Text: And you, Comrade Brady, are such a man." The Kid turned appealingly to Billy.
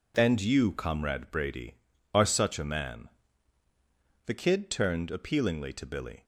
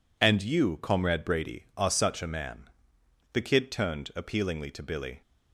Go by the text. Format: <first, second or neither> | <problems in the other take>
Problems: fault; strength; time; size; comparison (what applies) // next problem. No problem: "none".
neither | none